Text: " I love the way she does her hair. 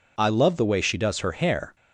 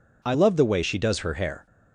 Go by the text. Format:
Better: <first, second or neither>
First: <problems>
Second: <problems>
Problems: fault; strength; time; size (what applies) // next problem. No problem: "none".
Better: neither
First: none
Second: none